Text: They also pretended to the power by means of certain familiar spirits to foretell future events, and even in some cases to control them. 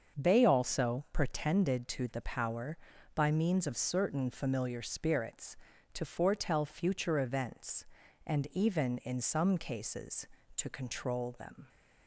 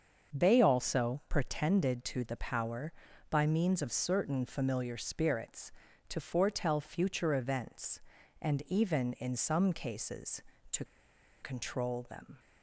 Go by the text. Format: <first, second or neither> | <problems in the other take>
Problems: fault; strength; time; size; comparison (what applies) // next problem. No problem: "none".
first | starts louder than the rest; until 1.4 s; 6.5 dB; also in the first // pauses between "to" and "control"; noticeable; at 10.8 s; 0.56 s long